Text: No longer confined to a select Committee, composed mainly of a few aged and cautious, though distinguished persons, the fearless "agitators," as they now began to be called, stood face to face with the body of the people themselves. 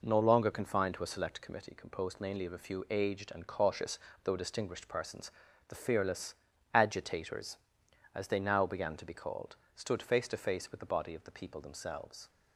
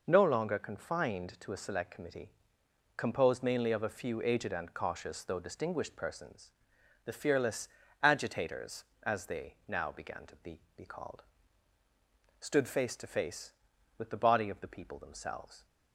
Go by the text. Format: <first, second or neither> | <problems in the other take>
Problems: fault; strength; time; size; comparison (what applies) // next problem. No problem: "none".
first | pauses between "fearless" and "agitators"; slight; at 7.6 s; 0.34 s long; also in the first // says "be" twice; at 10.7 s